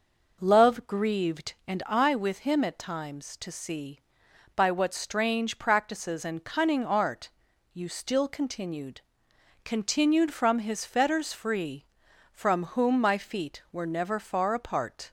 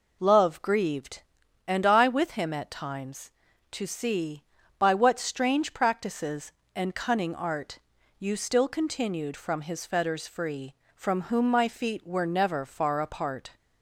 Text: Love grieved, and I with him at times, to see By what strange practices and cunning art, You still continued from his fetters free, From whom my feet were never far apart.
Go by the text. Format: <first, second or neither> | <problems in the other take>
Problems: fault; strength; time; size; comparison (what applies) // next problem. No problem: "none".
second | says "continued" twice; at 9.6 s